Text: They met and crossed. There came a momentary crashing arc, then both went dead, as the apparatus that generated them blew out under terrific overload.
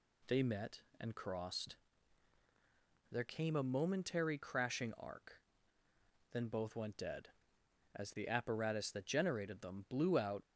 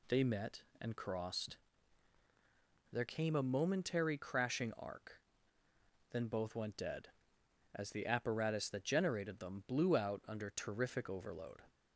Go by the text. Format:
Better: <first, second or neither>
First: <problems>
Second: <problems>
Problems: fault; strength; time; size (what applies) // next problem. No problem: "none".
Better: second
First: stops before "under terrific overload"; at 10.4 s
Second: none